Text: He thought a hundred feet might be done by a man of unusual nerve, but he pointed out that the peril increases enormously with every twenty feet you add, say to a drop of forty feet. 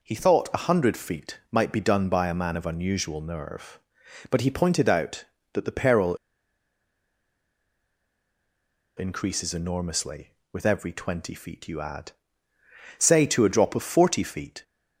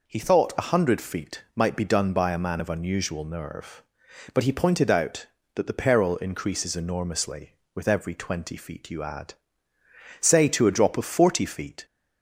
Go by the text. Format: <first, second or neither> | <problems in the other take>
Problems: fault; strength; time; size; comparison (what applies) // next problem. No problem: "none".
second | pauses between "peril" and "increases"; strong; at 6.1 s; 2.8 s long